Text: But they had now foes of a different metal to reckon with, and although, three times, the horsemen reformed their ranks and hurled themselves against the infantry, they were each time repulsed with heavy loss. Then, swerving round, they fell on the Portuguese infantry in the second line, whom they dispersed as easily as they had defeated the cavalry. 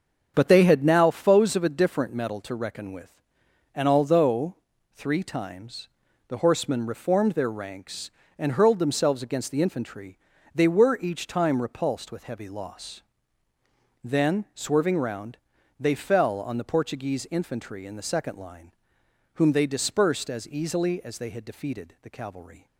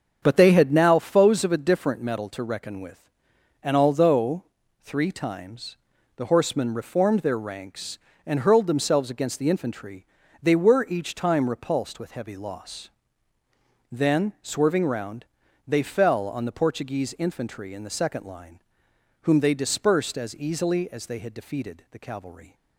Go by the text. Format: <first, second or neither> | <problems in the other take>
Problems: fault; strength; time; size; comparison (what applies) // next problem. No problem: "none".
neither | starts louder than the rest; the same in both